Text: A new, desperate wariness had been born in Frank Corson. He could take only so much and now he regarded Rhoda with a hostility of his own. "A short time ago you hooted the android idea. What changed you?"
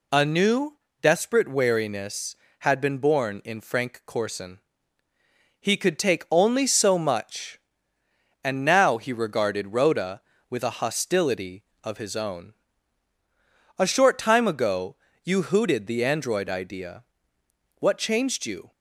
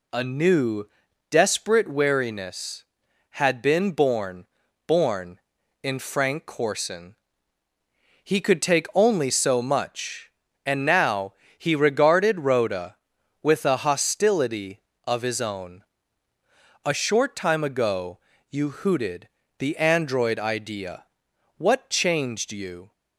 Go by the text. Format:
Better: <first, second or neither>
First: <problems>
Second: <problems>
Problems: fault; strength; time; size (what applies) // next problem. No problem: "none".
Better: first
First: pauses between "ago" and "you"; slight; at 14.9 s; 0.30 s long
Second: says "born" twice; at 4.8 s // pauses between "now" and "he"; slight; at 11.3 s; 0.24 s long // pauses between "ago" and "you"; slight; at 18.1 s; 0.32 s long // pauses between "hooted" and "the"; slight; at 19.2 s; 0.30 s long